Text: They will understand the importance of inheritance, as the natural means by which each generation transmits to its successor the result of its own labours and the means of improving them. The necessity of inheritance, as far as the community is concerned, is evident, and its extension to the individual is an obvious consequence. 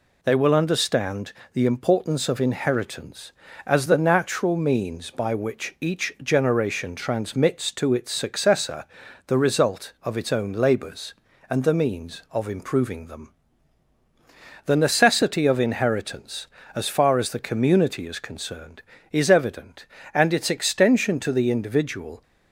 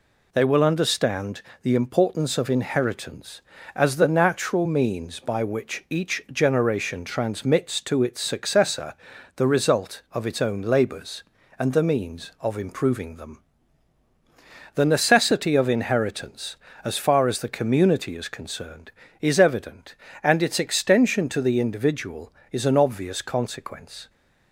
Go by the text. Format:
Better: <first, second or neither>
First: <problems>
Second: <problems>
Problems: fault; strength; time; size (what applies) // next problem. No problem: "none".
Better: second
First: pauses between "understand" and "the"; slight; at 1.3 s; 0.20 s long // pauses between "successor" and "the"; at 8.8 s; 0.44 s long // stops before "is an obvious consequence"; at 22.2 s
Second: pauses between "understand" and "the"; slight; at 1.4 s; 0.20 s long // pauses between "successor" and "the"; at 8.9 s; 0.44 s long